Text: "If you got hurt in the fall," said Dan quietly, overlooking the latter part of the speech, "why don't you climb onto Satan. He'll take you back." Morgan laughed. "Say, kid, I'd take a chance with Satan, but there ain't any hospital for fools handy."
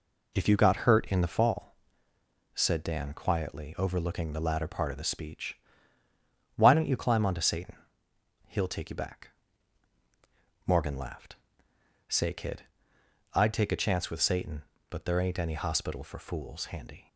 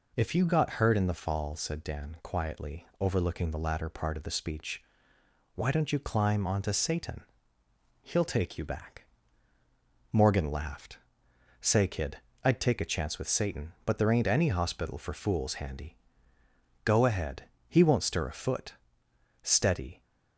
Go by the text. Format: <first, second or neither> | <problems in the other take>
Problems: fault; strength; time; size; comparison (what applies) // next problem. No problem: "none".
first | goes on to say "Go ahead He won't stir a foot Steady"; strong; from 16.8 s on; 3.1 s long